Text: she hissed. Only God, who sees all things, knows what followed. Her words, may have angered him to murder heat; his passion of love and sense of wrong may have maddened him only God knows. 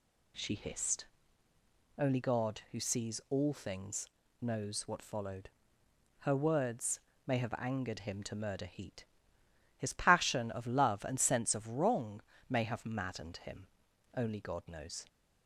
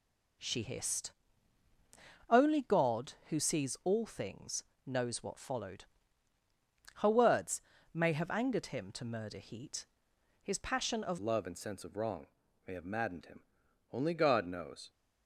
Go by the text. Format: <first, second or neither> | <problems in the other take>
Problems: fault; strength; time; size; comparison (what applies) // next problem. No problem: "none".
first | changes voice at "love"; from 11.1 s on; 3.7 s long // pauses between "wrong" and "may"; at 12.2 s; 0.40 s long; slight in the first // pauses between "him" and "only"; noticeable; at 13.4 s; 0.50 s long; noticeable in the first